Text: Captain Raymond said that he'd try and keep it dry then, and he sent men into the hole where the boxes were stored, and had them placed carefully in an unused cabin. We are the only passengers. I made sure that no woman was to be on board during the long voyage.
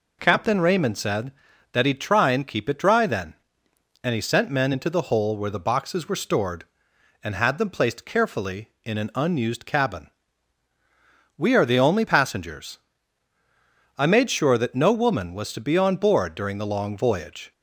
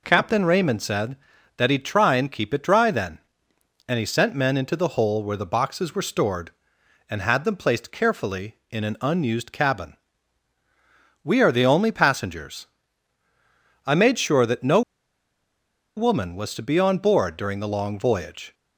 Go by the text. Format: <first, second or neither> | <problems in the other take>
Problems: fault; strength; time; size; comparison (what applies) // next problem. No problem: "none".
first | pauses between "no" and "woman"; at 14.8 s; 1.1 s long